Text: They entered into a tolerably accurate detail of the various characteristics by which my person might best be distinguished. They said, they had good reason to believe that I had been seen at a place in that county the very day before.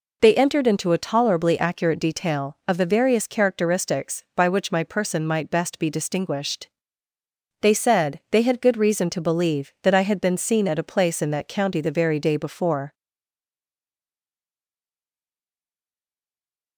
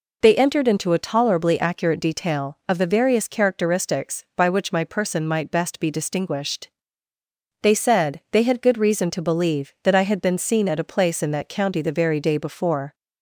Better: second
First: stays silent after the last word; strong; from 12.9 s on; 3.8 s long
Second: none

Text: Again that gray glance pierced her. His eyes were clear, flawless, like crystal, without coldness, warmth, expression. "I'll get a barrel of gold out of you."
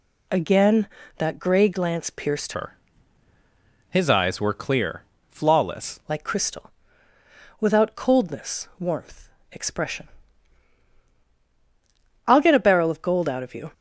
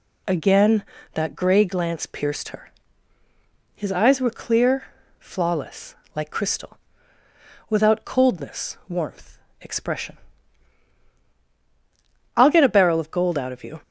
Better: second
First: changes voice from "her" to "flawless"; from 2.5 to 6.0 s; 3.5 s long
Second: none

